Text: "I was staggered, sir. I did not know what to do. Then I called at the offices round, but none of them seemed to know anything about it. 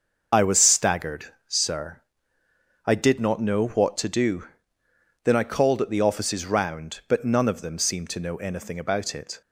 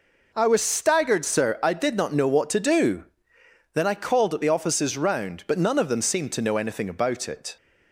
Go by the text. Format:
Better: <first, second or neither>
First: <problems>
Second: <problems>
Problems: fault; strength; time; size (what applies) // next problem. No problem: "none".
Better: second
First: loses the start of "I"; at 0.3 s; 35 ms // starts louder than the rest; noticeable; until 1.3 s; 6 dB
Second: none